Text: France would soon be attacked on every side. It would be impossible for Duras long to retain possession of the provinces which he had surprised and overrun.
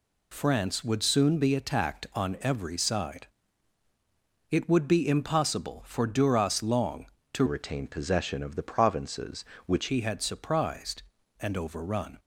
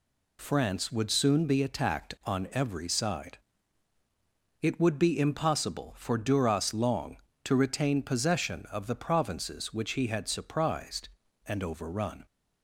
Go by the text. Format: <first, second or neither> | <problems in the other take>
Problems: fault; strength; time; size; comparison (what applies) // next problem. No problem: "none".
second | changes voice from "retain" to "which"; from 7.4 to 9.8 s; 2.4 s long